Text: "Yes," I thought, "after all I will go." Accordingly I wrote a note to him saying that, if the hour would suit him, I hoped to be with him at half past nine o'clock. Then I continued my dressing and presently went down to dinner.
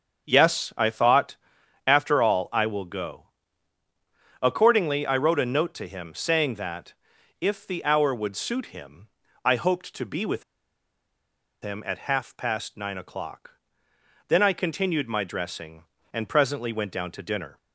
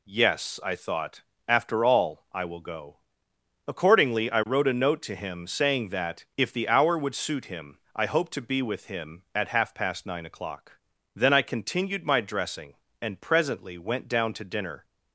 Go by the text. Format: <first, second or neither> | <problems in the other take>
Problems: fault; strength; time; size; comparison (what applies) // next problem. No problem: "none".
second | starts louder than the rest; until 1.3 s; 7 dB // pauses between "with" and "him"; at 10.4 s; 1.1 s long